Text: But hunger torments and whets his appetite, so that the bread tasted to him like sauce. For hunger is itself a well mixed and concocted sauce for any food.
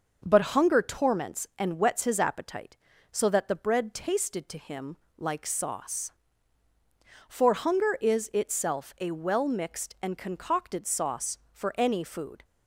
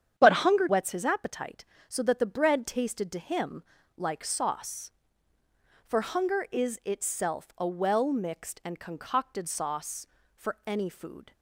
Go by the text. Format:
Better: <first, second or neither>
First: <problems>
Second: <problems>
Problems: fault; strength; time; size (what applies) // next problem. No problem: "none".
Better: first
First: pauses between "him" and "like"; slight; at 4.9 s; 0.20 s long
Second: starts louder than the rest; strong; until 1.1 s; 9 dB // skips "torments and"; at 0.6 s // pauses between "him" and "like"; slight; at 3.6 s; 0.34 s long